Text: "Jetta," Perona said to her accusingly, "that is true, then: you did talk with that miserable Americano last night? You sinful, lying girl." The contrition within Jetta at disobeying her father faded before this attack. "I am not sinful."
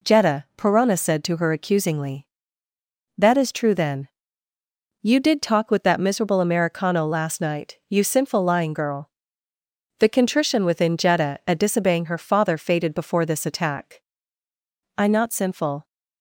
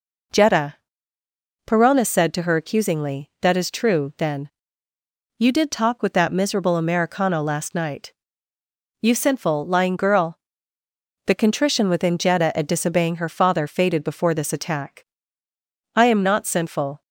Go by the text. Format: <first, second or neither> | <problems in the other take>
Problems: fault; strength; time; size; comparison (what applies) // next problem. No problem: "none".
second | skips "am"; at 15.0 s